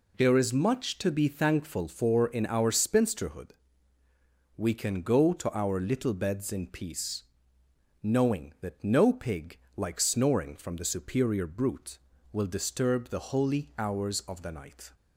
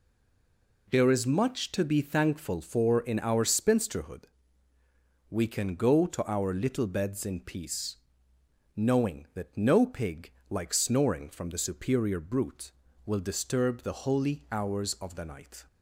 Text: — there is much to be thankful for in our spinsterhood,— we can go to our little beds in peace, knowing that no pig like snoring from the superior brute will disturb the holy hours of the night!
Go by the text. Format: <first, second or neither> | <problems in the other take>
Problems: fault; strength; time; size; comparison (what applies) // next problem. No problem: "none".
first | stays silent before the first word; slight; until 0.8 s; 0.8 s long // pauses between "pig" and "like"; slight; at 10.3 s; 0.18 s long; slight in the first